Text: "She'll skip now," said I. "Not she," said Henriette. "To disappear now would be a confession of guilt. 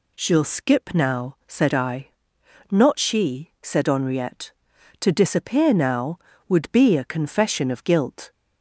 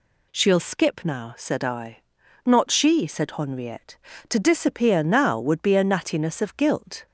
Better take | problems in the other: first | says "nattiness" for "confession"; at 5.8 s

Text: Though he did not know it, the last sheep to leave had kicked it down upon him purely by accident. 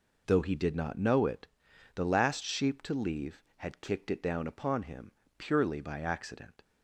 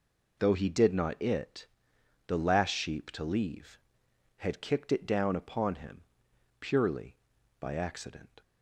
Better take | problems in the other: first | skips "know"; at 1.2 s // pauses between "him" and "purely"; noticeable; at 6.0 s; 0.58 s long; slight in the first

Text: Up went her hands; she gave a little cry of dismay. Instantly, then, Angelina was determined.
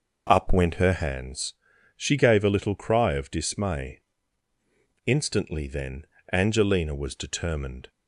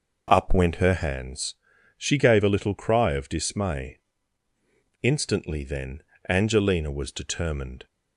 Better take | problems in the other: neither | none

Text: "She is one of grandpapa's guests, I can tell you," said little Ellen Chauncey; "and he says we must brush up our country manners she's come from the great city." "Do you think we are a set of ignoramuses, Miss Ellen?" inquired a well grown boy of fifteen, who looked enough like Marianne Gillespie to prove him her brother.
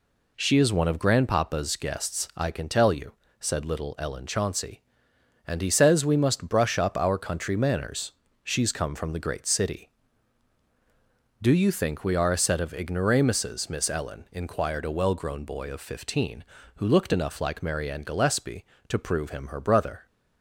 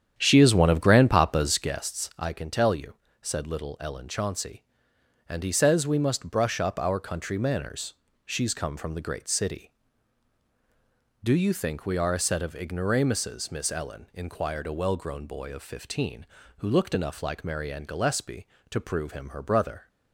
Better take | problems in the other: first | starts louder than the rest; strong; until 1.8 s; 9 dB // pauses between "manners" and "she's"; slight; at 7.9 s; 0.34 s long; slight in the first

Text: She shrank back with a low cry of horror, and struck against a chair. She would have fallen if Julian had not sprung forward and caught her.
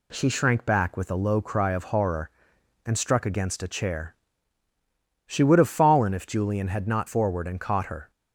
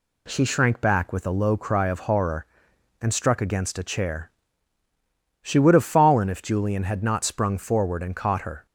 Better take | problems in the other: second | skips "sprung"; at 7.0 s

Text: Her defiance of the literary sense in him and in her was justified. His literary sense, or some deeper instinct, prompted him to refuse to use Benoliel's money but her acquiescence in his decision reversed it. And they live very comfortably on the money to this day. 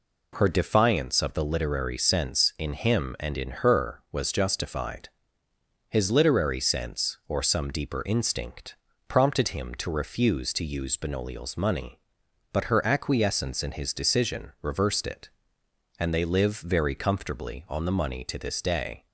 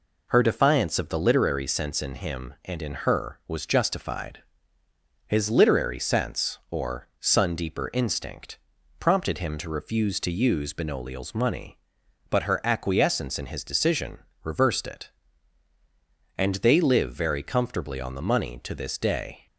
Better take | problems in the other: first | says "sun" for "some"; at 7.2 s // pauses between "decision" and "reversed"; slight; at 14.1 s; 0.24 s long

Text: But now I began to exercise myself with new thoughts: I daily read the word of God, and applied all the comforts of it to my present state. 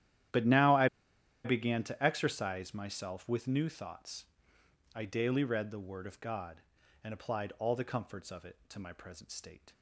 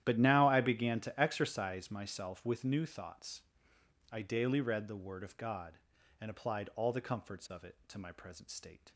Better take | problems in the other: second | starts louder than the rest; strong; until 1.9 s; 11.5 dB; strong in the second // pauses between "I" and "began"; noticeable; at 0.8 s; 0.57 s long

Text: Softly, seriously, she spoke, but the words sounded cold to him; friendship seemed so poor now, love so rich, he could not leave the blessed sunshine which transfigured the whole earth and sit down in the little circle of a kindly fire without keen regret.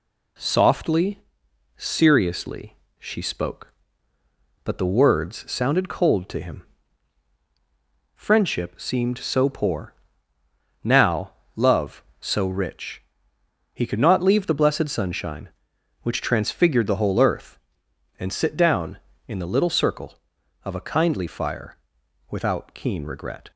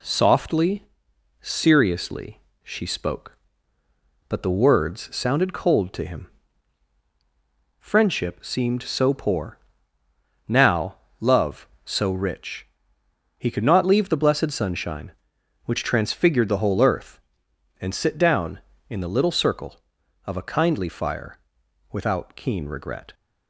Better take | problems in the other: neither | pauses between "poor" and "now"; noticeable; the same in both // pauses between "fire" and "without"; noticeable; the same in both

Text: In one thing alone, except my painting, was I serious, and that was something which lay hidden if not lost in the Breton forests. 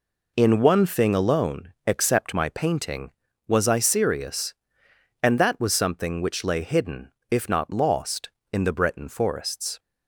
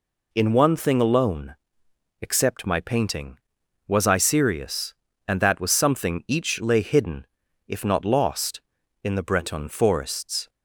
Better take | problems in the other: first | says "each" for "which"; at 6.2 s // pauses between "hidden" and "if"; at 7.2 s; 0.40 s long; slight in the first

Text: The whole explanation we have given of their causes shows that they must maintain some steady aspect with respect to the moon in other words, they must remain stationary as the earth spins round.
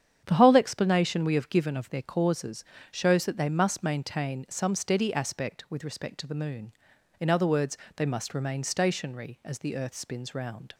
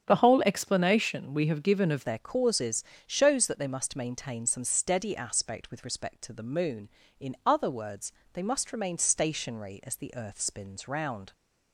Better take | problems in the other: first | starts louder than the rest; strong; until 1.0 s; 8 dB; strong in the first // changes voice at "their"; from 2.0 s on; 9.3 s long // pauses between "causes" and "shows"; slight; at 2.8 s; 0.22 s long; slight in the first

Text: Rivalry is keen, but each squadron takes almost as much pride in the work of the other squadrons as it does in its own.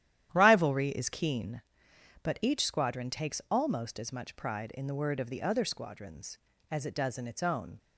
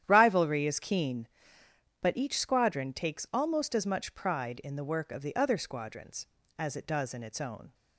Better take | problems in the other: second | starts louder than the rest; strong; until 1.3 s; 11.5 dB; strong in the second // says "word" for "work"; at 4.9 s

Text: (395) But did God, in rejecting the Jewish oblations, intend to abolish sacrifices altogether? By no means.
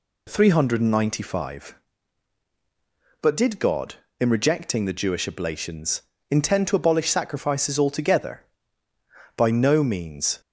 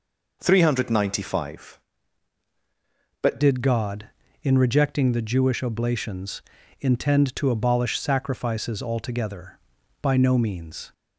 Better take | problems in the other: first | changes voice at "did"; from 3.4 s on; 7.5 s long

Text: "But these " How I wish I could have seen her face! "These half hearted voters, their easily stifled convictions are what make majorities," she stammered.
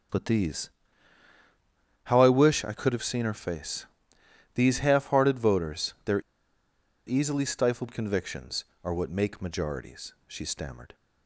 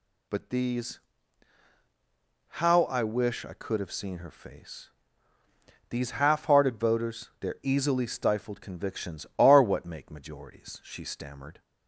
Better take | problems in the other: second | pauses between "their" and "easily"; noticeable; at 6.2 s; 0.86 s long

